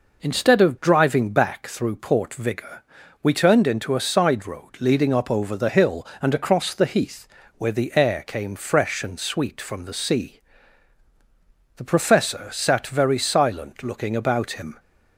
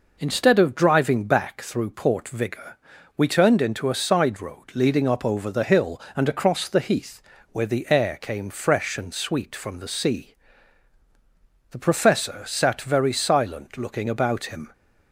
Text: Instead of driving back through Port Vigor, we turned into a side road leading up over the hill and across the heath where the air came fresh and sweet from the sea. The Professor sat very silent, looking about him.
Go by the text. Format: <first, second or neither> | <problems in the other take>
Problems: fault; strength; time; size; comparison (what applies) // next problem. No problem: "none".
neither | pauses between "heath" and "where"; slight; the same in both